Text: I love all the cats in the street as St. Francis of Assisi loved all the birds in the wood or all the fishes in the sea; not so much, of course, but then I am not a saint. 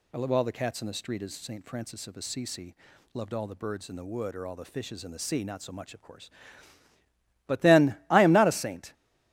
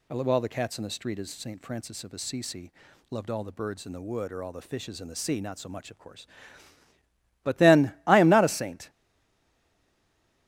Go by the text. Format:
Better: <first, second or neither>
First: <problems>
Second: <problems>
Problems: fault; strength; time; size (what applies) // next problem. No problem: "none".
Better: first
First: pauses between "Assisi" and "loved"; at 2.7 s; 0.38 s long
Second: pauses between "Assisi" and "loved"; at 2.7 s; 0.38 s long // stays silent after the last word; noticeable; from 8.8 s on; 1.6 s long